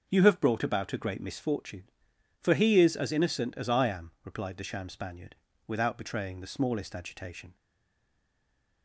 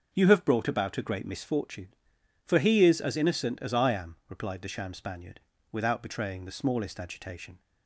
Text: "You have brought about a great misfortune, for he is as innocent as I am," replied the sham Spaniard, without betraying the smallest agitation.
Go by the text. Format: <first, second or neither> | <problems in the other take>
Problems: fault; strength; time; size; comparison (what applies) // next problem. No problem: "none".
second | starts louder than the rest; until 1.0 s; 6 dB; also in the second // stays silent after the last word; noticeable; from 7.5 s on; 1.3 s long